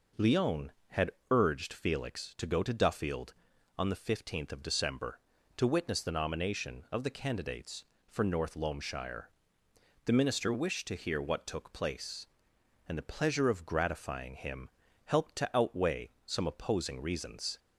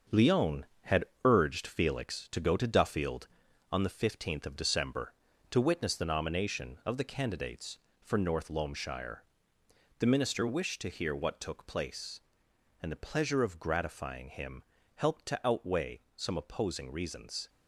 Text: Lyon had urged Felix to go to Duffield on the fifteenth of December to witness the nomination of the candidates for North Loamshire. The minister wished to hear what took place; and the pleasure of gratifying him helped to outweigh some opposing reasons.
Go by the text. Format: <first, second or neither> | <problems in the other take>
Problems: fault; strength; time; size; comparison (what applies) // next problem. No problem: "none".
first | gets quieter; strong; throughout; 7.5 dB // pauses between "had" and "urged"; slight; at 1.0 s; 0.22 s long; slight in the first // pauses between "him" and "helped"; slight; at 14.6 s; 0.30 s long; slight in the first // pauses between "outweigh" and "some"; slight; at 15.9 s; 0.16 s long; slight in the first